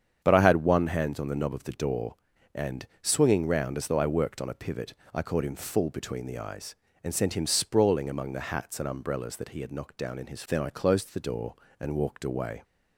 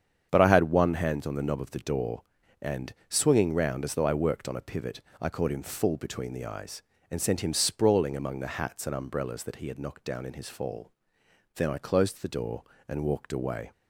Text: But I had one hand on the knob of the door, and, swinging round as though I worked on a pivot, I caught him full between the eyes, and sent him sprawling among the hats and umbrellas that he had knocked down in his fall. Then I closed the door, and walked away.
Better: second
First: starts louder than the rest; strong; until 1.2 s; 8 dB // skips "fall"; at 10.4 s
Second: starts louder than the rest; strong; until 1.3 s; 8 dB

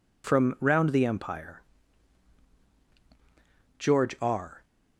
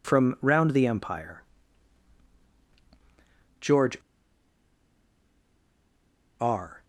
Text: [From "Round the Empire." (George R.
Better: first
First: none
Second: pauses between "George" and "R"; strong; at 3.9 s; 2.4 s long

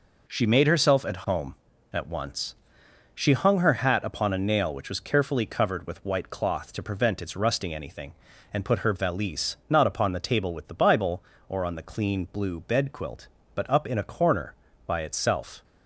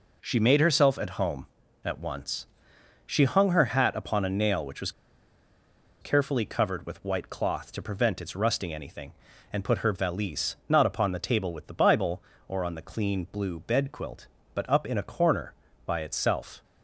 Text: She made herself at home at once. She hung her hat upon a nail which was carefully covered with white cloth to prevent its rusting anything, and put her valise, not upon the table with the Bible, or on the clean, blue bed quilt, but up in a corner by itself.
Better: first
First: none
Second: pauses between "was" and "carefully"; at 4.9 s; 1.1 s long

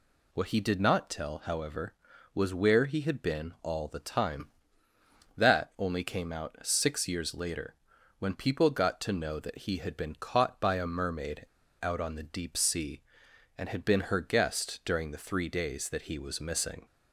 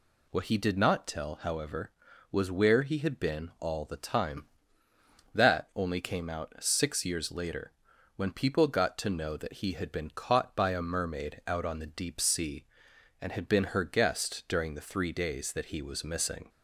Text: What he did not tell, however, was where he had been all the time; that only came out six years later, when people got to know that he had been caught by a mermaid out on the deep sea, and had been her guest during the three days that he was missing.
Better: second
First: pauses between "mermaid" and "out"; at 11.4 s; 0.36 s long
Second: none

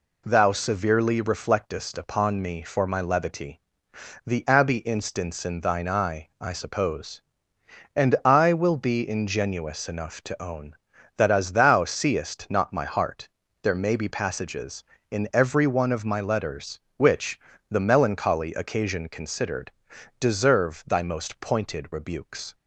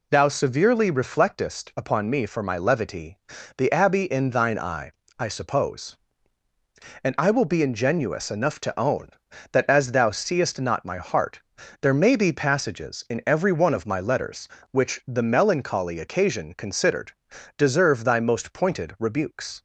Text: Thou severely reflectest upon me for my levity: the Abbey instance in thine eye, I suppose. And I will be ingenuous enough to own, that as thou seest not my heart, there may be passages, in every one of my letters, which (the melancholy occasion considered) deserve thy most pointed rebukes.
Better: first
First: none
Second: skips "instance"; at 4.0 s

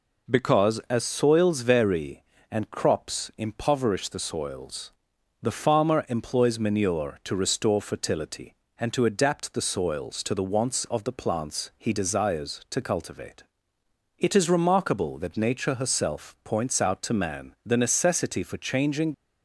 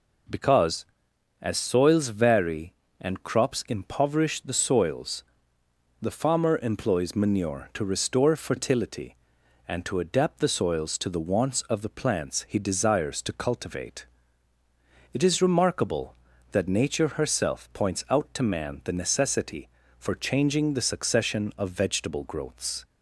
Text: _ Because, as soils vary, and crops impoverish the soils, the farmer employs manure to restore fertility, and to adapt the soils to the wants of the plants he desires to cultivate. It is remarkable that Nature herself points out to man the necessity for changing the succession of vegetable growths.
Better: second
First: stops before "the succession of vegetable growths"; at 19.1 s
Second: none

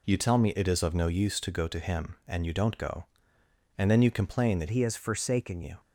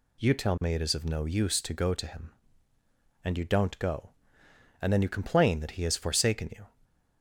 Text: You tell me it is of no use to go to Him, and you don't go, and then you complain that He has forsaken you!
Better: second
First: changes voice from "He" to "forsaken"; from 4.7 to 5.6 s; 0.9 s long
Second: none

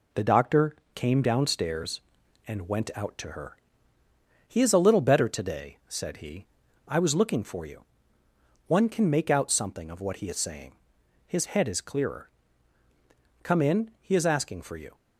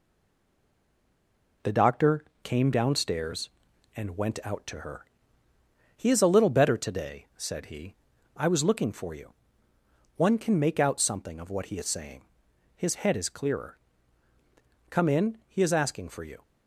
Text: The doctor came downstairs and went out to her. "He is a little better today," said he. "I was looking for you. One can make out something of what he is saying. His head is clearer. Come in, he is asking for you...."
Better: first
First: pauses between "doctor" and "came"; slight; at 0.7 s; 0.18 s long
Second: stays silent before the first word; noticeable; until 1.6 s; 1.6 s long // pauses between "doctor" and "came"; slight; at 2.2 s; 0.18 s long

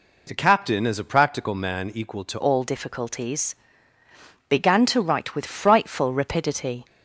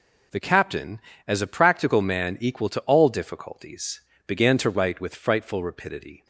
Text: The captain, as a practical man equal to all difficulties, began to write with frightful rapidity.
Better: second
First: changes voice at "all"; from 2.4 s on; 4.4 s long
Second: none

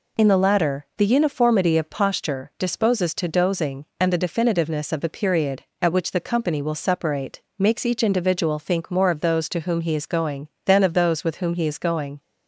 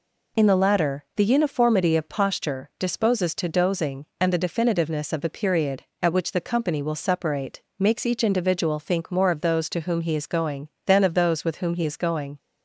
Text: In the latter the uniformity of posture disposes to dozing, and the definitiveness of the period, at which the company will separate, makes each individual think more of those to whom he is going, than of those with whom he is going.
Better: neither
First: none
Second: none

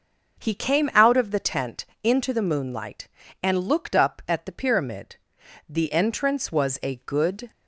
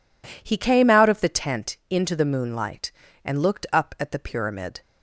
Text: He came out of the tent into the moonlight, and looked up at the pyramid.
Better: second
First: starts louder than the rest; until 1.4 s; 6.5 dB // pauses between "tent" and "into"; slight; at 1.8 s; 0.20 s long // goes on to say "The entrance was a good"; strong; from 5.6 s on; 1.8 s long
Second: none

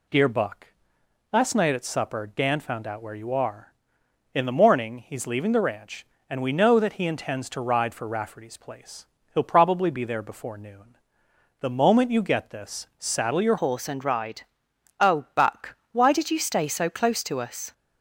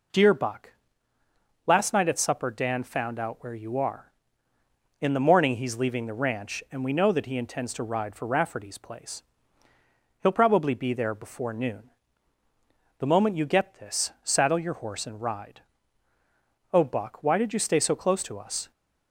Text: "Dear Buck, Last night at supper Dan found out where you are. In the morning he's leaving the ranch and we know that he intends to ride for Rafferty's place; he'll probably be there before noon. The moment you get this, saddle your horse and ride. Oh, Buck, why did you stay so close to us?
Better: second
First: changes voice at "horse"; from 13.5 s on; 4.2 s long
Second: none

